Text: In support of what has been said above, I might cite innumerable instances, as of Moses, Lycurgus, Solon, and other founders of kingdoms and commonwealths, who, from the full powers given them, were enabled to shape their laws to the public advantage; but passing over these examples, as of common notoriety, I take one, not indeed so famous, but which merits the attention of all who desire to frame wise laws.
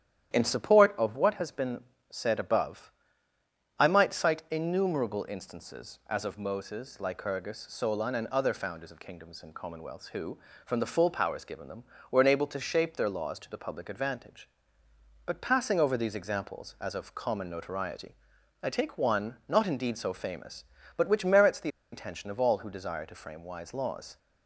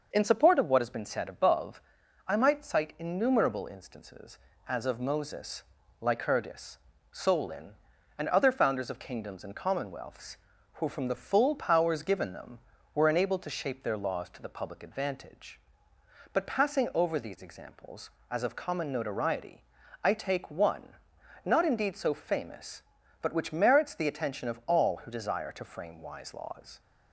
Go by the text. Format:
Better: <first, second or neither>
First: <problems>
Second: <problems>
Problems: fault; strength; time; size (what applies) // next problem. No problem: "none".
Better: second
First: starts louder than the rest; strong; until 1.3 s; 10.5 dB // pauses between "been" and "said"; slight; at 1.8 s; 0.30 s long // pauses between "the" and "attention"; slight; at 21.6 s; 0.24 s long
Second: none